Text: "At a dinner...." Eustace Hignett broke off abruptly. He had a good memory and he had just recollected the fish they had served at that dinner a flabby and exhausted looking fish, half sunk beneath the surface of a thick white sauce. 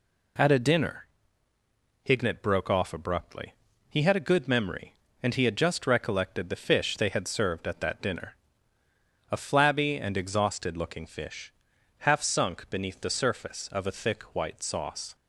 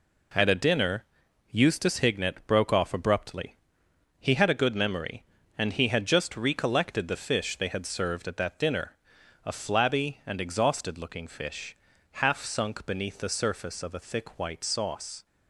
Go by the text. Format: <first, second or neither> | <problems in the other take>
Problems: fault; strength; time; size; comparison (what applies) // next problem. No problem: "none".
second | skips "Eustace"; at 1.5 s // pauses between "dinner" and "a"; noticeable; at 8.3 s; 0.96 s long; noticeable in the second